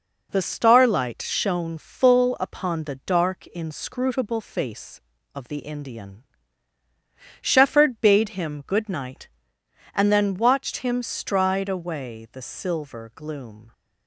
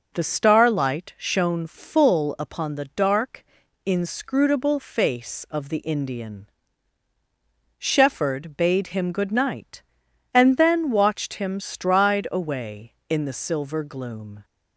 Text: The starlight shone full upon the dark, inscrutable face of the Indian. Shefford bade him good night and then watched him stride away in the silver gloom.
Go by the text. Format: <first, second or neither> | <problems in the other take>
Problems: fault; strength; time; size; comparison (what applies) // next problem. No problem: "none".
second | skips "in"; at 12.2 s